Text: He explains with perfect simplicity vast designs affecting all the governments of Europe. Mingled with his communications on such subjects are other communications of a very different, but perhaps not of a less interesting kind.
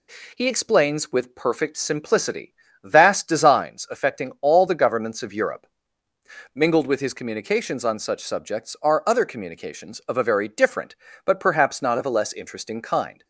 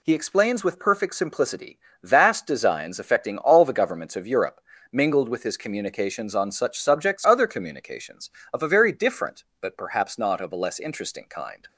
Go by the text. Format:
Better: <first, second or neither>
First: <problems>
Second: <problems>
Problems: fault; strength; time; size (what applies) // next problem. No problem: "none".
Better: first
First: pauses between "simplicity" and "vast"; slight; at 2.5 s; 0.30 s long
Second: pauses between "simplicity" and "vast"; slight; at 1.7 s; 0.24 s long // skips "are"; at 7.2 s